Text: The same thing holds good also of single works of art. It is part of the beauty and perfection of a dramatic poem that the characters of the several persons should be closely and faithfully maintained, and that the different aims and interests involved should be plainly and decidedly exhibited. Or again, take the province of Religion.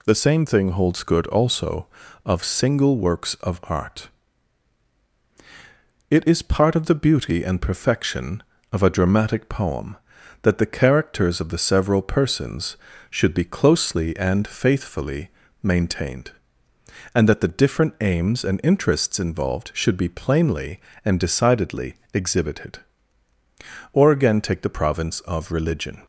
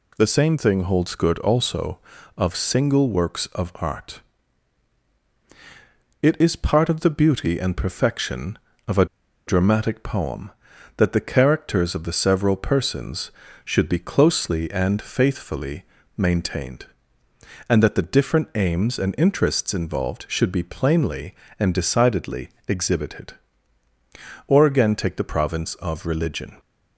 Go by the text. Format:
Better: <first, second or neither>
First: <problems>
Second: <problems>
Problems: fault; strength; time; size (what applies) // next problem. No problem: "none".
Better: first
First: pauses between "faithfully" and "maintained"; slight; at 15.3 s; 0.32 s long // pauses between "decidedly" and "exhibited"; slight; at 21.9 s; 0.20 s long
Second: pauses between "a" and "dramatic"; at 9.0 s; 0.41 s long // pauses between "faithfully" and "maintained"; slight; at 15.8 s; 0.32 s long // pauses between "decidedly" and "exhibited"; slight; at 22.4 s; 0.20 s long